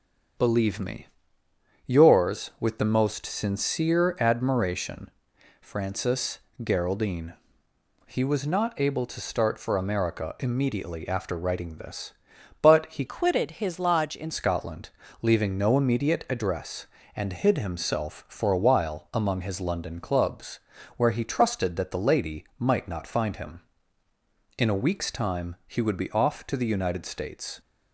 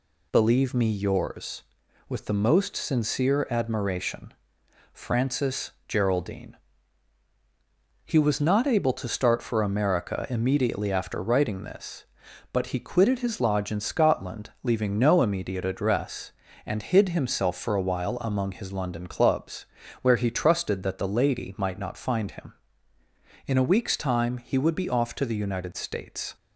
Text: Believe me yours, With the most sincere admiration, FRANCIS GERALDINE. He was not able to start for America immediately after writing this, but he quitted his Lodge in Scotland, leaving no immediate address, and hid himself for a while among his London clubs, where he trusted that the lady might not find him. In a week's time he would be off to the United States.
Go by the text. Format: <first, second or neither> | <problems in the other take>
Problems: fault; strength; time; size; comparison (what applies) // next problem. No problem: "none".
second | starts louder than the rest; strong; until 2.1 s; 7 dB // pauses between "me" and "yours"; noticeable; at 1.0 s; 0.78 s long // pauses between "FRANCIS" and "GERALDINE"; slight; at 6.3 s; 0.24 s long; slight in the second // changes voice from "quitted" to "in"; from 13.0 to 14.2 s; 1.2 s long